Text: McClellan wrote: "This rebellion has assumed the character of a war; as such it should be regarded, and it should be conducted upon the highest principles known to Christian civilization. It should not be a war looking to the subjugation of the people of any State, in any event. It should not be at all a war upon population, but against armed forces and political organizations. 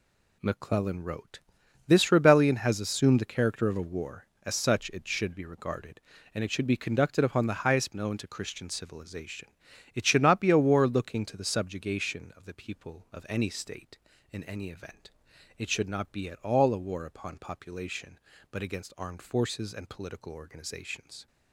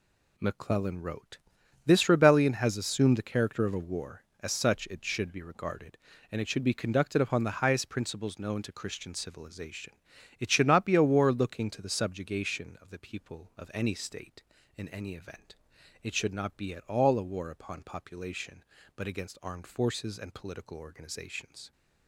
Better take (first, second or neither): second